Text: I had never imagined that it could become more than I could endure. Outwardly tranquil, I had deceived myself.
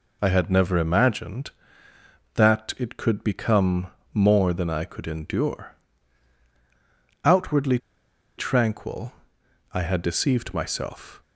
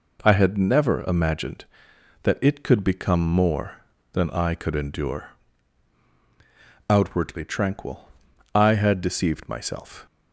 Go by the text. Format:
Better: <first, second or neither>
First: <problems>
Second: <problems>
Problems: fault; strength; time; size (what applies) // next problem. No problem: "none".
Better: second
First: pauses between "become" and "more"; slight; at 3.8 s; 0.26 s long // pauses between "Outwardly" and "tranquil"; noticeable; at 7.7 s; 0.60 s long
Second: none